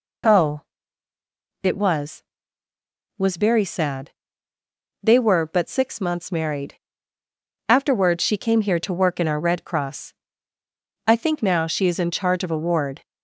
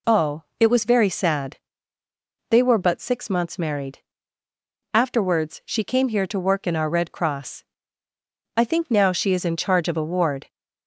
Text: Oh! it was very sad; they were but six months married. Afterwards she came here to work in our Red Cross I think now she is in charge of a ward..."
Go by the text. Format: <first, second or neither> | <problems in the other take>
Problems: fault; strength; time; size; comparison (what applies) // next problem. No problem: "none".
second | says "was" twice; at 3.1 s // pauses between "Cross" and "I"; noticeable; at 10.1 s; 0.92 s long; noticeable in the second